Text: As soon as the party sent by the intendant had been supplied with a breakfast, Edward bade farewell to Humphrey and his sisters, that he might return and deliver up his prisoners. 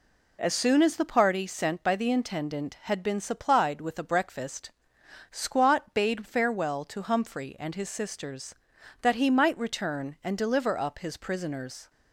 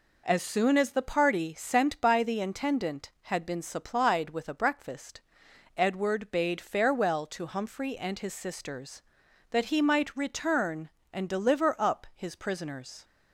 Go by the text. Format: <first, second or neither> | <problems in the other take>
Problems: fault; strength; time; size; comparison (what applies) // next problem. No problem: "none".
second | says "Squat" for "Edward"; at 5.2 s